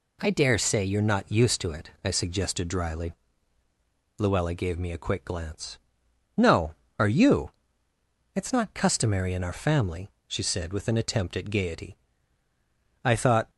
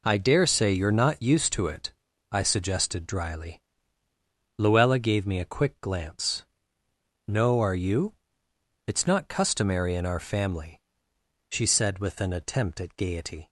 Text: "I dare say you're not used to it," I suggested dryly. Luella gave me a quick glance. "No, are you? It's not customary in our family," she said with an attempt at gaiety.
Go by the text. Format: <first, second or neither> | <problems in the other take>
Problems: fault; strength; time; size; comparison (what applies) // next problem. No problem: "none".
second | goes on to say "I thought"; slight; from 13.0 s on; 0.48 s long